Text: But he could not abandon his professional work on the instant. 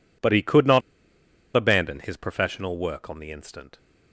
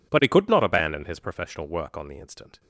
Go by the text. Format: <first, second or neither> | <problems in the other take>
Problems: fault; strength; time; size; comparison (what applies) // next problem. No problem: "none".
second | pauses between "not" and "abandon"; noticeable; at 0.8 s; 0.74 s long